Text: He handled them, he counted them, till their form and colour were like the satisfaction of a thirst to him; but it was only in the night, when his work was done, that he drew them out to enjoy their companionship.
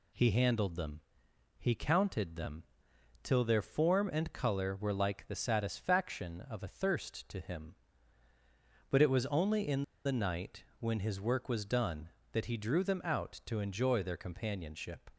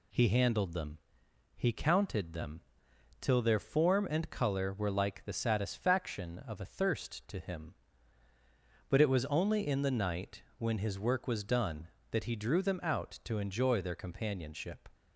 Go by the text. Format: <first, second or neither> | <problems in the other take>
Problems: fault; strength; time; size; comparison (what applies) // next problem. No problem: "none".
second | pauses between "in" and "the"; slight; at 9.8 s; 0.24 s long